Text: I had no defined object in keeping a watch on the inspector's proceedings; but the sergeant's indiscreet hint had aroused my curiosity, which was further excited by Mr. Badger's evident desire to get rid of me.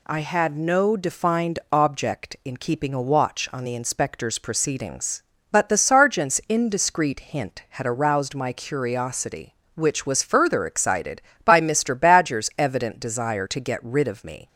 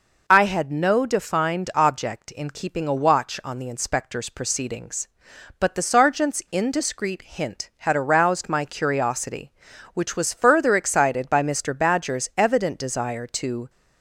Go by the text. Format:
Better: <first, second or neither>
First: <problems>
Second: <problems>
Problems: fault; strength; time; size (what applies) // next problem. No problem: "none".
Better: first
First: none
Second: stops before "get rid of me"; at 13.6 s